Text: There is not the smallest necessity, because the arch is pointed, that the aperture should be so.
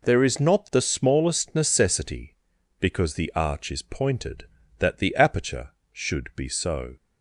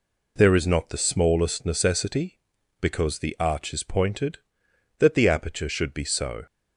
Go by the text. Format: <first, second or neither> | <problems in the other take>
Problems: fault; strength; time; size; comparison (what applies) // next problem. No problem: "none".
neither | none